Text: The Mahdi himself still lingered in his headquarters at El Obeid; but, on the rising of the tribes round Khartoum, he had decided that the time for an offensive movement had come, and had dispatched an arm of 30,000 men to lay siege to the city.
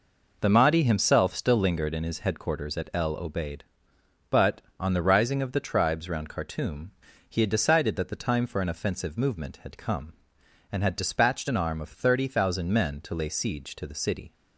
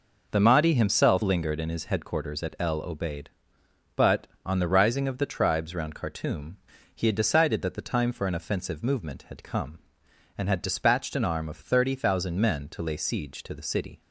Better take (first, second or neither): first